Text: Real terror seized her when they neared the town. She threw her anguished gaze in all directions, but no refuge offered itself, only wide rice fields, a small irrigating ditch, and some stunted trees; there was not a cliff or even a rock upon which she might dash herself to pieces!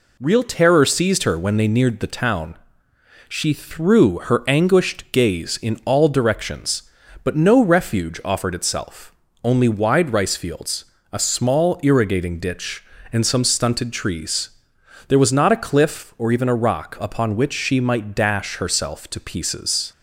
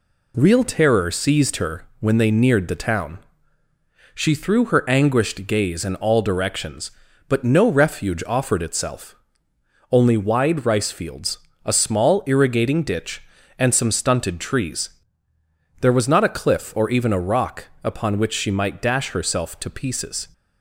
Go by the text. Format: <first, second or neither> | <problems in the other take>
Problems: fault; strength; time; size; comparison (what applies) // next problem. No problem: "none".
neither | none